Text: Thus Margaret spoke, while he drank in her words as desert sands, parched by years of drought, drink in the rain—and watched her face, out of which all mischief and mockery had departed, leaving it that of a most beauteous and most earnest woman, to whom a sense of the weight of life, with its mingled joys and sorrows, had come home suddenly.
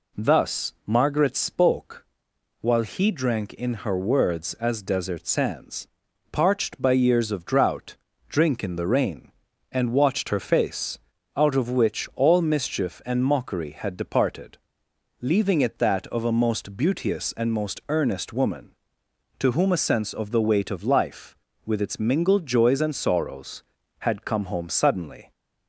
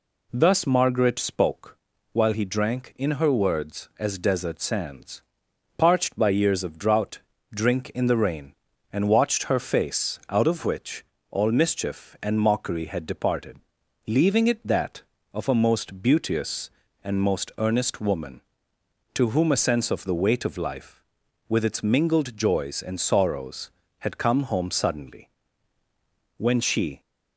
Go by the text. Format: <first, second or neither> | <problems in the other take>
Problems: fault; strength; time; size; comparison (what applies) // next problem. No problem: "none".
first | pauses between "which" and "all"; slight; at 11.0 s; 0.28 s long // goes on to say "When she"; noticeable; from 26.3 s on; 0.64 s long